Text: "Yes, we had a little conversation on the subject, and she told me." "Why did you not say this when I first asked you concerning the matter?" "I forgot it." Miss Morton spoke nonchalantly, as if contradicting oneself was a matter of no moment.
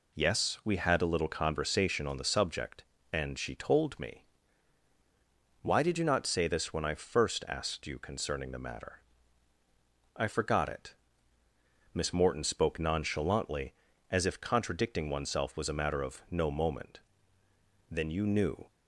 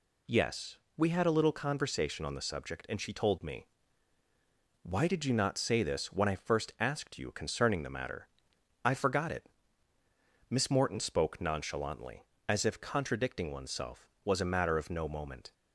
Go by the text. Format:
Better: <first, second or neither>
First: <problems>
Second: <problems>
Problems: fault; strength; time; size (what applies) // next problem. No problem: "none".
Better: second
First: goes on to say "Then you knew"; noticeable; from 17.9 s on; 0.80 s long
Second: none